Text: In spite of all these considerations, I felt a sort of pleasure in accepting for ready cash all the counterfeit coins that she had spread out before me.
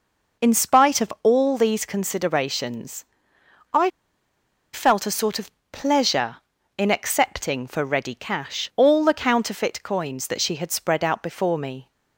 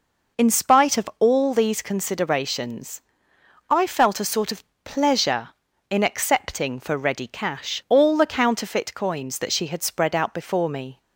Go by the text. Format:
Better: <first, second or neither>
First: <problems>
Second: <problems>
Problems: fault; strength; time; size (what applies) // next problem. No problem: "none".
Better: second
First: pauses between "I" and "felt"; noticeable; at 3.8 s; 0.83 s long // pauses between "of" and "pleasure"; slight; at 5.5 s; 0.20 s long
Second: pauses between "of" and "pleasure"; slight; at 4.6 s; 0.20 s long